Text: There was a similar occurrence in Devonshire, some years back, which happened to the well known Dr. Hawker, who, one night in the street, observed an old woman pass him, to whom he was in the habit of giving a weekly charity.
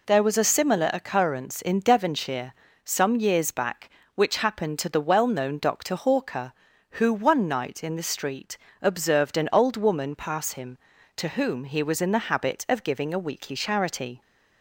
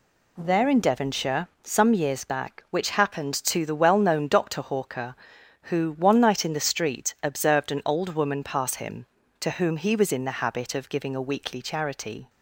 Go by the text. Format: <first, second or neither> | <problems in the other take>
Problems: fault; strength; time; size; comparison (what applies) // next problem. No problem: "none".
first | skips "was a similar occurrence"; at 0.6 s